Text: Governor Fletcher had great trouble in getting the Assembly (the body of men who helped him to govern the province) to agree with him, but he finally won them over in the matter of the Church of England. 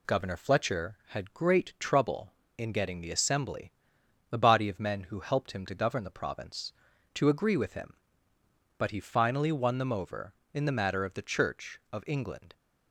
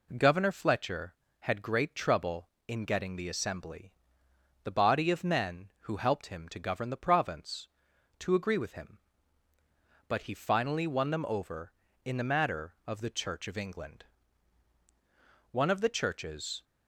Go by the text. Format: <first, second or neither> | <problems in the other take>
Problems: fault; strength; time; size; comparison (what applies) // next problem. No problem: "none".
first | goes on to say "One of the churches"; noticeable; from 15.5 s on; 1.1 s long